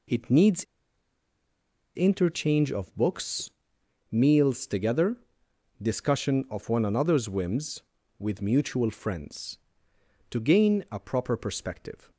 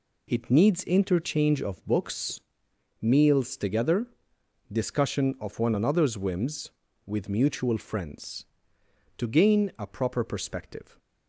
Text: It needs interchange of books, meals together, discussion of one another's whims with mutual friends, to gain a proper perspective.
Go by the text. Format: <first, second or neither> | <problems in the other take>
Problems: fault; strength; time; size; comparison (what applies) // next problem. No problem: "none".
second | pauses between "needs" and "interchange"; strong; at 0.6 s; 1.3 s long